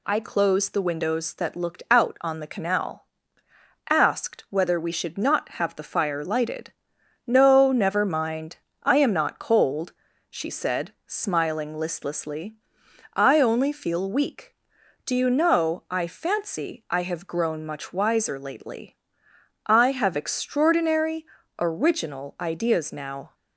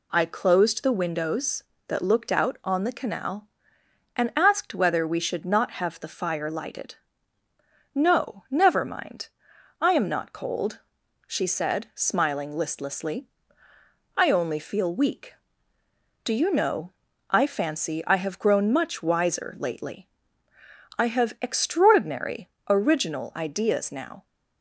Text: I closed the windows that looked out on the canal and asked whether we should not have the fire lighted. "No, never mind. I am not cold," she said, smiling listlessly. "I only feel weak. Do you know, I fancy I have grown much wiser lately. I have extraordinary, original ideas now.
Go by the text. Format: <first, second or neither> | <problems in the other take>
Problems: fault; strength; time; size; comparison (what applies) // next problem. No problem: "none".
second | skips "and"; at 3.4 s